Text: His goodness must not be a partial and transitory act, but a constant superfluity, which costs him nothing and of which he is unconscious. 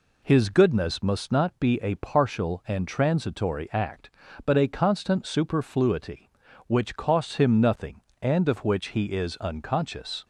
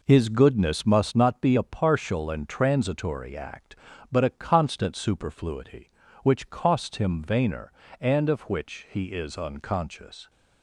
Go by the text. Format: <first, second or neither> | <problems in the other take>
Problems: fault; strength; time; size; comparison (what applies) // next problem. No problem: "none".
first | says "vainer" for "nothing"; at 7.2 s